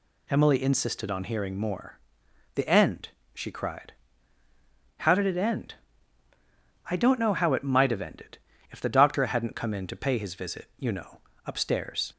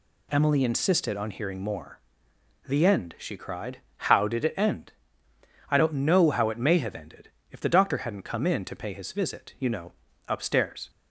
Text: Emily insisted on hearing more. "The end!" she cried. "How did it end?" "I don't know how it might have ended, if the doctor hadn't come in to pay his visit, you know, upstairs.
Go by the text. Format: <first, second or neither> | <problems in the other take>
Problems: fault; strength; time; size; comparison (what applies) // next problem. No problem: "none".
first | says "may" for "might"; at 6.5 s